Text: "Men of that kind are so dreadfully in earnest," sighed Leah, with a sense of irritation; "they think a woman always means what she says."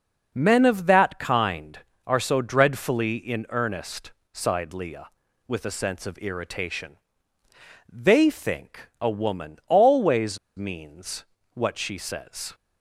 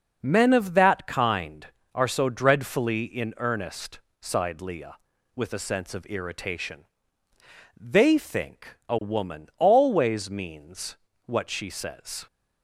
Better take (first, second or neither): second